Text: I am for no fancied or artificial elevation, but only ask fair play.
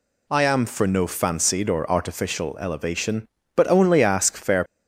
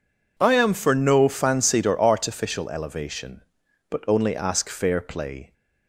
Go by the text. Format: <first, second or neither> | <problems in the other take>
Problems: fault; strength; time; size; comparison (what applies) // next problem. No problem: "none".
second | stops before "play"; at 4.6 s